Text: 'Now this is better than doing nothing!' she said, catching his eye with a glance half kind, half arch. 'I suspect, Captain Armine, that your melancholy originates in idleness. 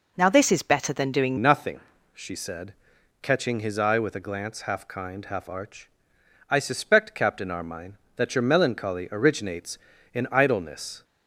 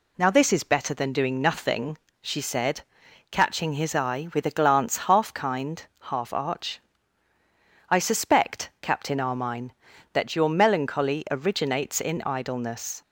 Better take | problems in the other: second | changes voice at "nothing"; from 1.3 s on; 9.7 s long

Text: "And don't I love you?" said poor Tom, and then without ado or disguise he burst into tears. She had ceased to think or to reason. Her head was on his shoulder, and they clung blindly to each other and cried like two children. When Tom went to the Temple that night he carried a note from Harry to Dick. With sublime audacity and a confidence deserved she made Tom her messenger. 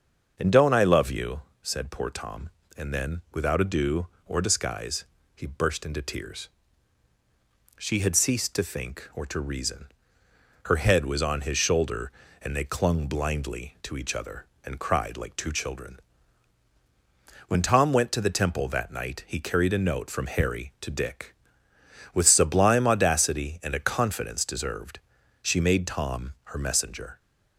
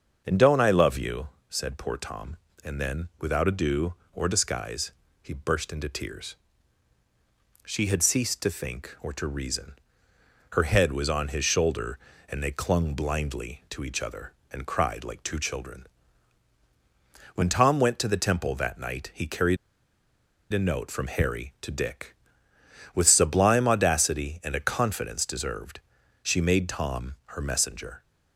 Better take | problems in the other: first | starts louder than the rest; until 1.2 s; 6.5 dB; also in the first // pauses between "disguise" and "he"; slight; at 4.9 s; 0.30 s long; slight in the first // pauses between "carried" and "a"; noticeable; at 19.5 s; 0.95 s long // pauses between "deserved" and "she"; at 25.8 s; 0.42 s long; also in the first

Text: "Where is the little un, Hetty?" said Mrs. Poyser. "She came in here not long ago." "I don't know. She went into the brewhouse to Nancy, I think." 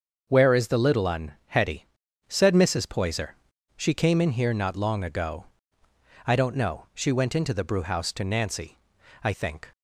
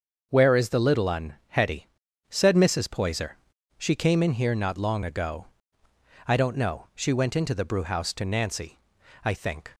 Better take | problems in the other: neither | starts louder than the rest; the same in both

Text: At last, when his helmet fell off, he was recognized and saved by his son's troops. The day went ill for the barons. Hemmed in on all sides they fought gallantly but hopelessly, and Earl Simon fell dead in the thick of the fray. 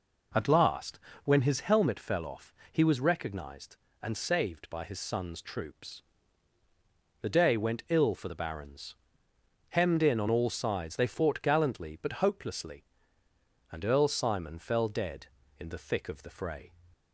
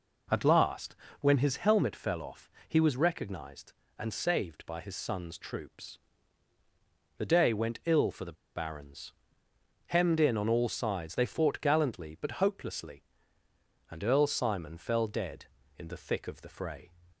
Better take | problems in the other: first | pauses between "the" and "barons"; slight; at 8.3 s; 0.22 s long

